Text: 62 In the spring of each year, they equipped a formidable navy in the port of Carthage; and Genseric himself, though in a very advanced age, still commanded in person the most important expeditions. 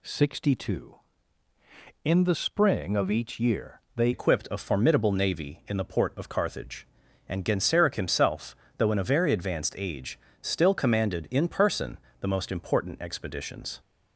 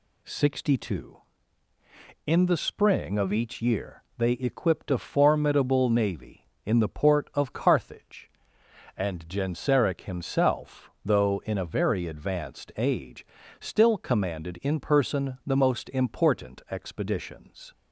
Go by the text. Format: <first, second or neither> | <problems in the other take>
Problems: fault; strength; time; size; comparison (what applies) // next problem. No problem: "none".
second | changes voice at "equipped"; from 4.1 s on; 9.6 s long // pauses between "person" and "the"; slight; at 11.9 s; 0.24 s long